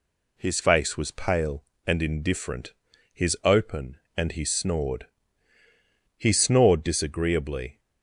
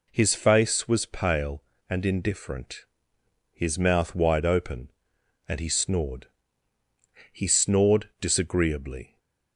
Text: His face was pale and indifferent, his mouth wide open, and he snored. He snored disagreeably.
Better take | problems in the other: second | skips "mouth wide"; at 3.3 s

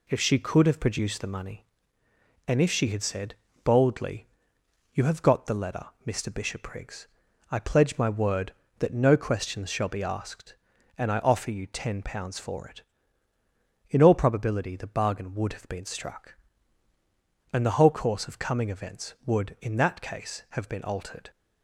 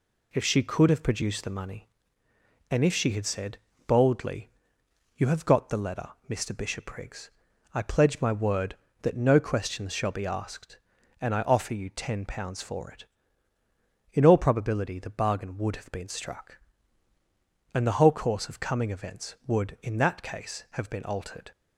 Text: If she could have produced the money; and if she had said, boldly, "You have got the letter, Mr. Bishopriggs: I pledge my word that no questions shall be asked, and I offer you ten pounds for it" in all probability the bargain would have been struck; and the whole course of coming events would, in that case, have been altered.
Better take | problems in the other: neither | none

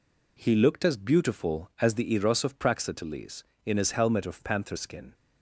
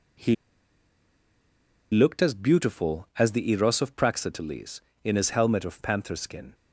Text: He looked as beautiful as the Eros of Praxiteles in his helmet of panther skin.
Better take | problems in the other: first | pauses between "He" and "looked"; strong; at 0.3 s; 1.5 s long

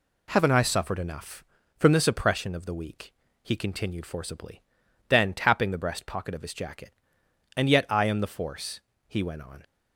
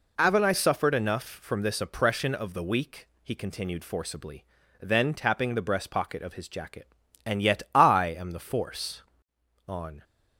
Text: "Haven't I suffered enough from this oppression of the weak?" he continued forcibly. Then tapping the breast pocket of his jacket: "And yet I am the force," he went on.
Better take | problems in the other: first | skips "he went"; at 9.3 s

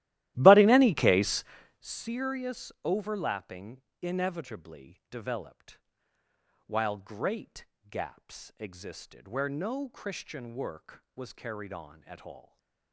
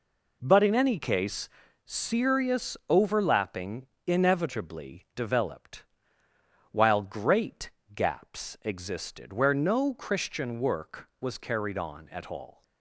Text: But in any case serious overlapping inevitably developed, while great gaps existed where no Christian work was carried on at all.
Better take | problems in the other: second | starts louder than the rest; strong; until 2.0 s; 15 dB // pauses between "case" and "serious"; slight; at 1.4 s; 0.36 s long; slight in the second // pauses between "overlapping" and "inevitably"; slight; at 3.8 s; 0.20 s long; slight in the second // pauses between "great" and "gaps"; slight; at 7.6 s; 0.26 s long; slight in the second // stays silent after the last word; slight; from 12.4 s on; 0.5 s long

